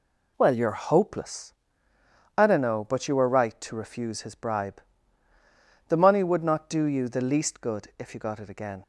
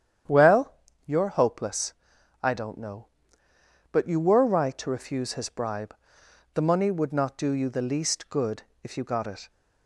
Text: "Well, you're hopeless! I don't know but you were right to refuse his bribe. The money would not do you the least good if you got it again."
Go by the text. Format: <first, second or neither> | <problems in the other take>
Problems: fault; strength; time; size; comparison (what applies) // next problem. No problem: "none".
first | starts louder than the rest; strong; until 1.6 s; 9.5 dB // pauses between "good" and "if"; slight; at 8.6 s; 0.18 s long // stops before "again"; at 9.4 s